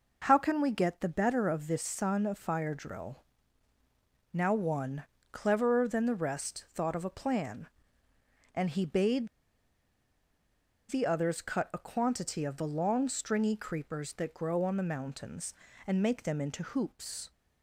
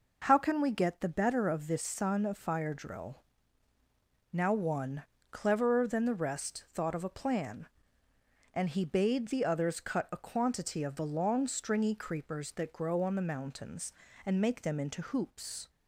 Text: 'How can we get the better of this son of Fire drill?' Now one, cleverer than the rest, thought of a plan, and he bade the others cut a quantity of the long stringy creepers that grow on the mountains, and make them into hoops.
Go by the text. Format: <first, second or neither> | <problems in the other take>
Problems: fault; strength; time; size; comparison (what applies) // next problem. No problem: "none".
second | pauses between "bade" and "the"; strong; at 9.2 s; 1.6 s long